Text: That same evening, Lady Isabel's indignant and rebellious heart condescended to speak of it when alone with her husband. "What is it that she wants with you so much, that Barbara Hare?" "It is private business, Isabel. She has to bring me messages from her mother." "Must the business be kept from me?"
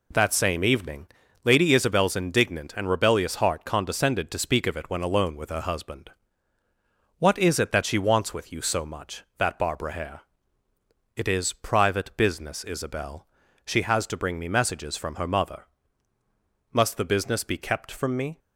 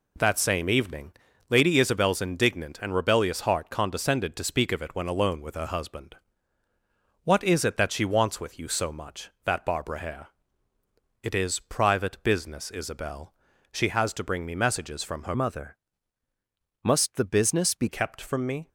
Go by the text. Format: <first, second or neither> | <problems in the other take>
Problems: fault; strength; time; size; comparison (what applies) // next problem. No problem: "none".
first | changes voice from "mother" to "be"; from 15.3 to 17.8 s; 2.5 s long